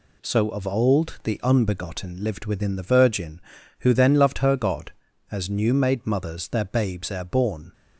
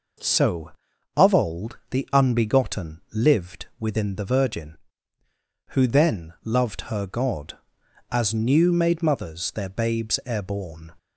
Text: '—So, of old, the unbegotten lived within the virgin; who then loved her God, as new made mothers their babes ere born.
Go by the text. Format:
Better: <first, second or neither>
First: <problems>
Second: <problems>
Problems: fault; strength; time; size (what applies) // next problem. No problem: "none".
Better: neither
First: none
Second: none